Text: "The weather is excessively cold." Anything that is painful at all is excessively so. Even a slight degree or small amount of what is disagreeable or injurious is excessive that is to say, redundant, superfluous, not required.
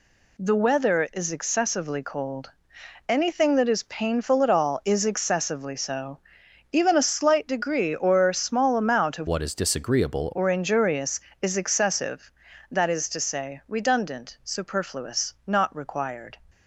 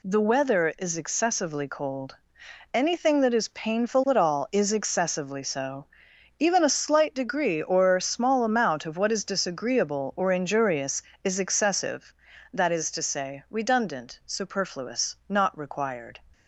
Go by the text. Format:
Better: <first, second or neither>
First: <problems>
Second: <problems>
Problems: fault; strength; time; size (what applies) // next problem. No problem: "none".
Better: second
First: changes voice from "what" to "disagreeable"; from 9.2 to 10.2 s; 1.0 s long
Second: none